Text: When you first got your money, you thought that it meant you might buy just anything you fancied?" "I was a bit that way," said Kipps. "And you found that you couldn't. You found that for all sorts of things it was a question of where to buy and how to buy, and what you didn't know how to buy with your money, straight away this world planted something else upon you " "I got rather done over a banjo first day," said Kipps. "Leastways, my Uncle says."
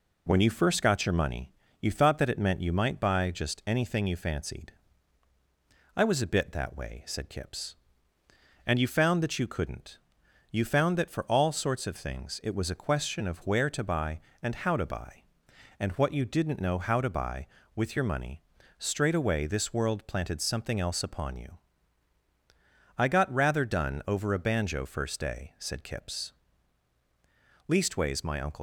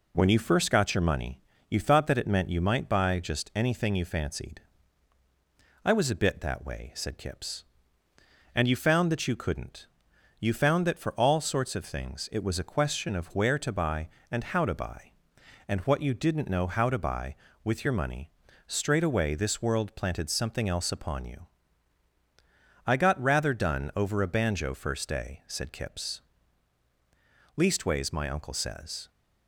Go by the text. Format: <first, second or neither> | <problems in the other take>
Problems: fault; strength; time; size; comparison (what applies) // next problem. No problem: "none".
second | stops before "says"; at 28.5 s